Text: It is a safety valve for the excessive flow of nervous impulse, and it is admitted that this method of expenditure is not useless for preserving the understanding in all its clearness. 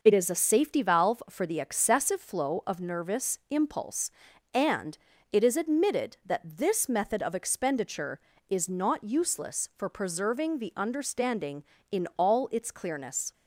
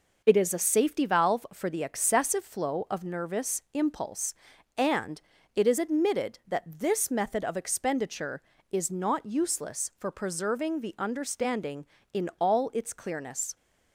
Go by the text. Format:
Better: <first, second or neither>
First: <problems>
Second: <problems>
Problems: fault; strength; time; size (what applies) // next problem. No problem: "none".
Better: neither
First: pauses between "and" and "it"; slight; at 4.9 s; 0.36 s long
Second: pauses between "and" and "it"; slight; at 5.2 s; 0.36 s long